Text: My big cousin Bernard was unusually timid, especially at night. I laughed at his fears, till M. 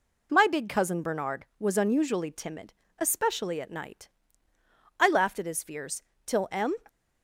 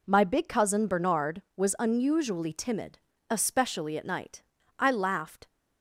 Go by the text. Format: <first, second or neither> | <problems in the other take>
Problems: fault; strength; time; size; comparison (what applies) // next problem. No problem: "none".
first | stops before "at his fears till M"; at 5.4 s